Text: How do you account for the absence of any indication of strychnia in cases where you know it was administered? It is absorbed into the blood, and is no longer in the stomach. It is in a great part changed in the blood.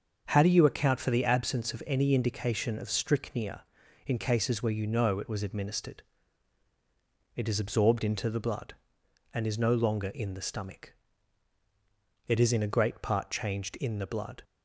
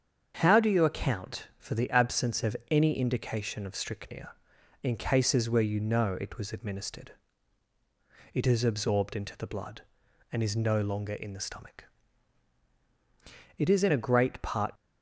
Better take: first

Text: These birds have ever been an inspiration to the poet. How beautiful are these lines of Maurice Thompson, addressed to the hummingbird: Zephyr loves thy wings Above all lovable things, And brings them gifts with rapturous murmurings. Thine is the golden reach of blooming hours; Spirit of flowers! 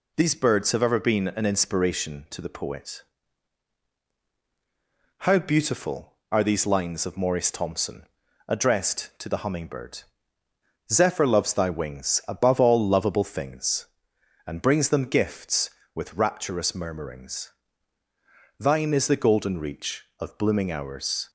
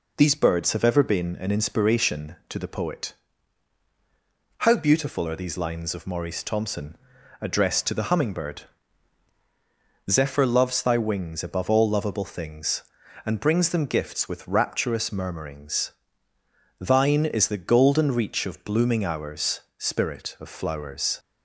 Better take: second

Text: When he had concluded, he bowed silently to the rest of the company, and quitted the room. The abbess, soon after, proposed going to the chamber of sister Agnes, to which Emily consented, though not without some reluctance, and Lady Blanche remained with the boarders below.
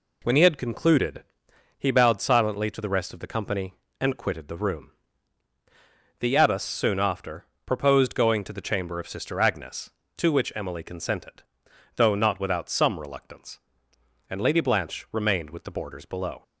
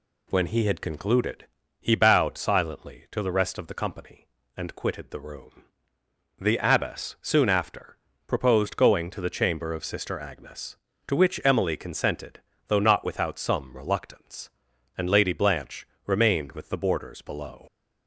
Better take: first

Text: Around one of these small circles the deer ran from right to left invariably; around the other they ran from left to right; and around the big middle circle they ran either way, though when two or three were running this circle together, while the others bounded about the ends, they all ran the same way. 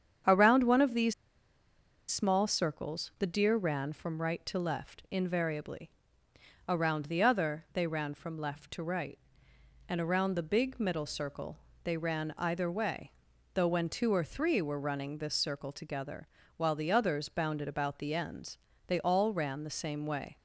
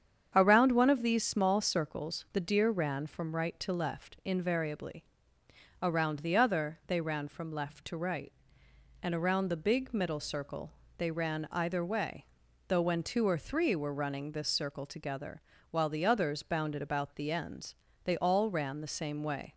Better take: second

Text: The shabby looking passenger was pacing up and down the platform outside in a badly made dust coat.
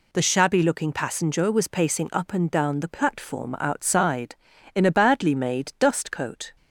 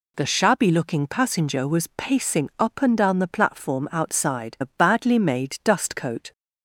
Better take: first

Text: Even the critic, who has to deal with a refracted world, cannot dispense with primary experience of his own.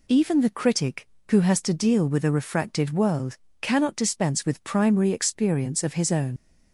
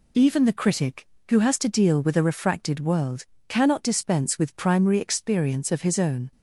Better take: second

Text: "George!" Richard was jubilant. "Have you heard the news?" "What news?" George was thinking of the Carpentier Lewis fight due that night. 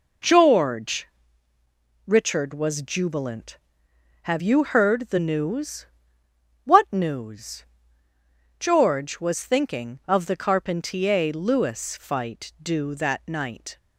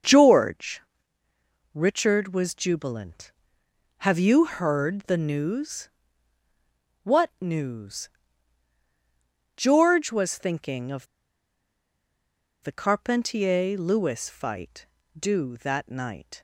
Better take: first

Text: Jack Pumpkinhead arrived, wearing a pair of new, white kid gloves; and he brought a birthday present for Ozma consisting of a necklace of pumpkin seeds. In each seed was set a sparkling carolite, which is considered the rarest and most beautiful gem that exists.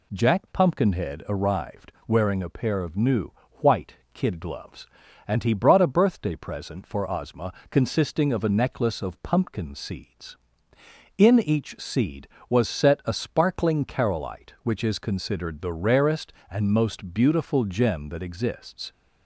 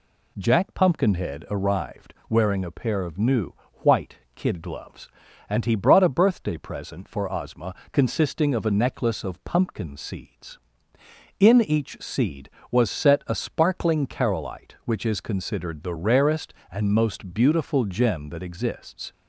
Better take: neither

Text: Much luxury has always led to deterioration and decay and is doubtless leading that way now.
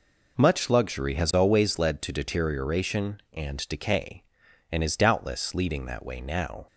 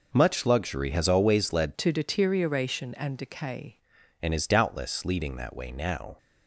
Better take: first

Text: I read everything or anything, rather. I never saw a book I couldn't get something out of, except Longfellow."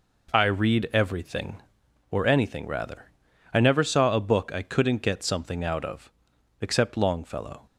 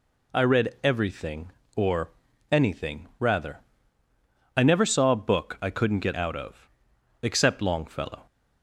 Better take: first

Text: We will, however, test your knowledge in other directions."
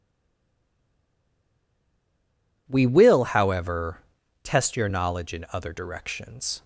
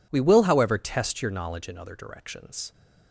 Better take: second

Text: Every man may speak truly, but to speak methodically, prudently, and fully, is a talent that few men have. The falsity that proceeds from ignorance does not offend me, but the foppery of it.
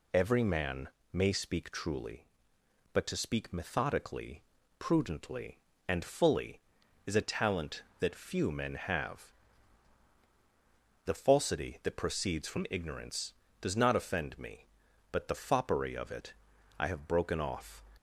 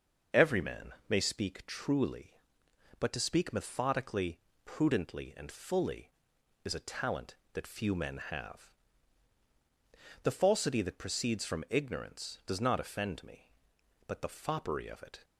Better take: second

